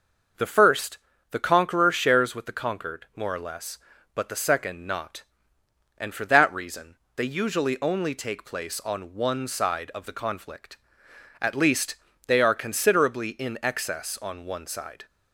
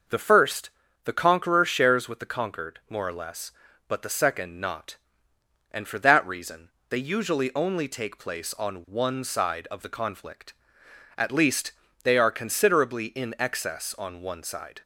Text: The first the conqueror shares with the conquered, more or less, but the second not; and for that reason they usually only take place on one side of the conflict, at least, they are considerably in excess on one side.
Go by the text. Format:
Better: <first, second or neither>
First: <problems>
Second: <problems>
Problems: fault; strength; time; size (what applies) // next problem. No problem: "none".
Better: neither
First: pauses between "first" and "the"; slight; at 0.9 s; 0.32 s long // pauses between "reason" and "they"; slight; at 6.9 s; 0.22 s long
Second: pauses between "first" and "the"; slight; at 0.6 s; 0.34 s long // pauses between "reason" and "they"; slight; at 6.6 s; 0.22 s long